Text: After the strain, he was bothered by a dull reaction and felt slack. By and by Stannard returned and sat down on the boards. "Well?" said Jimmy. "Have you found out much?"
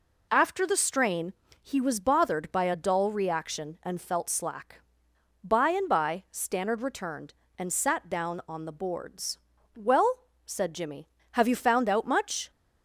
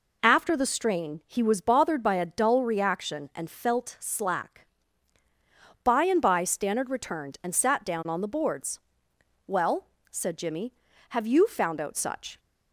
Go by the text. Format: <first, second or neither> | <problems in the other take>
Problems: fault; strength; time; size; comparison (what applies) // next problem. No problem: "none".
first | says "such" for "much"; at 11.9 s